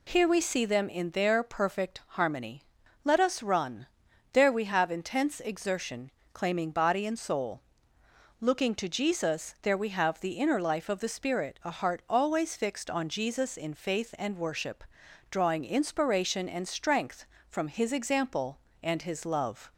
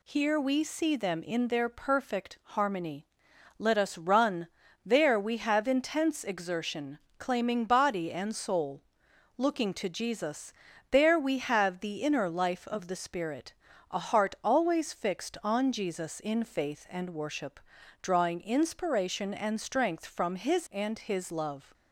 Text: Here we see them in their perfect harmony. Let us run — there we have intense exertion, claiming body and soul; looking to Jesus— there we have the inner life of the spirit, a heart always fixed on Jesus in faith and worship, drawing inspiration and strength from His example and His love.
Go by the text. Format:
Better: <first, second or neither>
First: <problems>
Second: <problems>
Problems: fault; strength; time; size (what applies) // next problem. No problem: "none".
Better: first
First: none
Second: skips "example"; at 20.6 s